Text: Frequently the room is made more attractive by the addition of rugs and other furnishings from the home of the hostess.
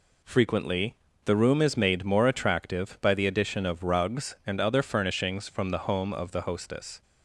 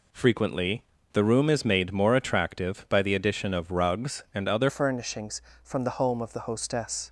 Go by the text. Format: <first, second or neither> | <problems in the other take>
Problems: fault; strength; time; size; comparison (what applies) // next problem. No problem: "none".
first | pauses between "Frequently" and "the"; slight; at 0.8 s; 0.30 s long; slight in the first // changes voice at "furnishings"; from 4.6 s on; 2.4 s long